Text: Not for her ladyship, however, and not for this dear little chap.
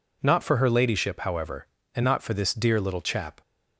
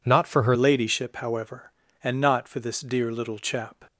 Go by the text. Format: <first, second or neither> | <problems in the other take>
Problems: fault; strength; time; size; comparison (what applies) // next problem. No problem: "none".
first | changes voice at "ladyship"; from 0.5 s on; 3.3 s long